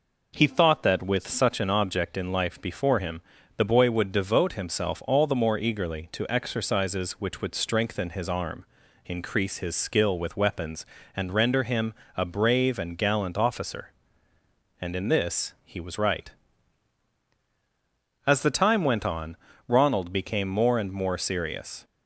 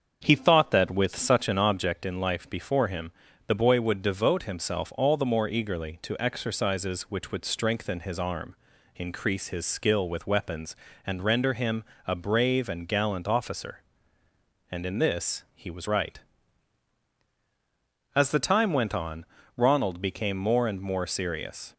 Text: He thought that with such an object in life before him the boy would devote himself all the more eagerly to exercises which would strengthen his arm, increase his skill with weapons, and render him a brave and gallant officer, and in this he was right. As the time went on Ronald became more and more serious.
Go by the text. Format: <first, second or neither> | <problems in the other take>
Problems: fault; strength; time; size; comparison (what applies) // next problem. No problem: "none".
first | starts louder than the rest; until 2.0 s; 7 dB // pauses between "him" and "the"; at 3.1 s; 0.38 s long; also in the first // pauses between "him" and "a"; slight; at 11.8 s; 0.24 s long; slight in the first // pauses between "on" and "Ronald"; slight; at 19.2 s; 0.32 s long; slight in the first